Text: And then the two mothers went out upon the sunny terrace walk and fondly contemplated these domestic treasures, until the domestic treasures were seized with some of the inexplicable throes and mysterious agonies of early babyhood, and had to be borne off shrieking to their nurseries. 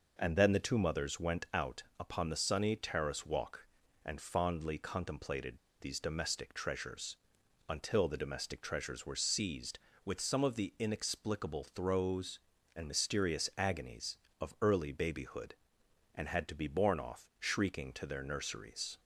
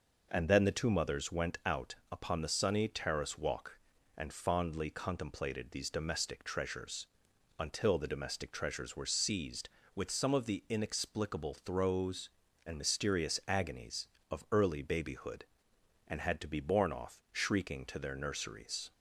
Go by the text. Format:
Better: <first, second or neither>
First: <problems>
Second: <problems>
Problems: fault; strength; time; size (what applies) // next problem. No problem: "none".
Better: second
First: pauses between "out" and "upon"; slight; at 1.8 s; 0.16 s long // pauses between "contemplated" and "these"; slight; at 5.5 s; 0.23 s long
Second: pauses between "out" and "upon"; slight; at 1.9 s; 0.16 s long